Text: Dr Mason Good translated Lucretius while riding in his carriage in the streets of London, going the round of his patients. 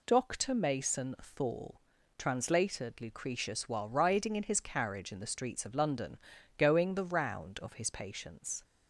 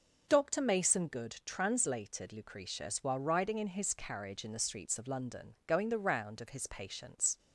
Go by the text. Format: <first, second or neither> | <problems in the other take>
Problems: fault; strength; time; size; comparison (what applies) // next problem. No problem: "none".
second | says "Thorl" for "Good"; at 1.2 s